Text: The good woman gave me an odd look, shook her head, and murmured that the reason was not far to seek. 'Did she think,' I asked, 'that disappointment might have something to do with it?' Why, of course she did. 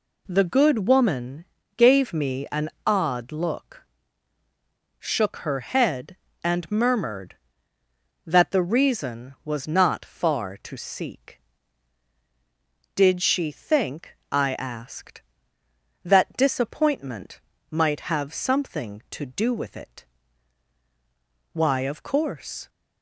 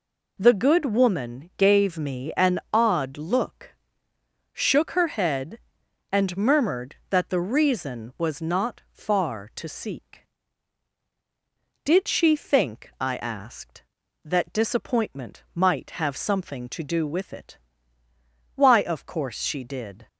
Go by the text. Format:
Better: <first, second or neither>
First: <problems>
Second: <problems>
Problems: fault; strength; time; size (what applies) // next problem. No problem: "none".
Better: second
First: pauses between "woman" and "gave"; slight; at 1.4 s; 0.32 s long // pauses between "an" and "odd"; slight; at 2.6 s; 0.16 s long // pauses between "disappointment" and "might"; slight; at 17.4 s; 0.30 s long // stops before "she did"; at 22.6 s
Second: none